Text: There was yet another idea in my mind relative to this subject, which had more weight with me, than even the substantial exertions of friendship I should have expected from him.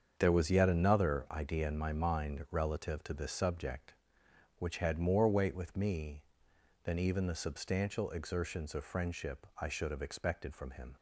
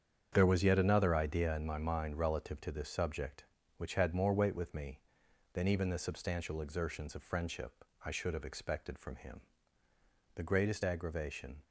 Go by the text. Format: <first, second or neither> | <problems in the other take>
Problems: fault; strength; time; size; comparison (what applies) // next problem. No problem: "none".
first | starts louder than the rest; strong; until 1.3 s; 8 dB; strong in the first // pauses between "friendship" and "I"; slight; at 7.8 s; 0.22 s long // goes on to say "The greatest aggravation"; noticeable; from 10.3 s on; 1.2 s long